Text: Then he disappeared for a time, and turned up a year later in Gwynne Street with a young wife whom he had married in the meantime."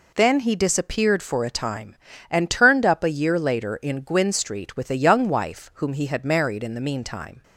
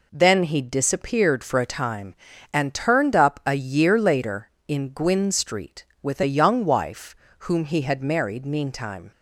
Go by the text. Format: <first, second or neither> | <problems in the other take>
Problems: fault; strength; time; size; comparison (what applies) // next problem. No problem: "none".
first | pauses between "wife" and "whom"; slight; at 7.1 s; 0.24 s long // skips "in the"; at 8.4 s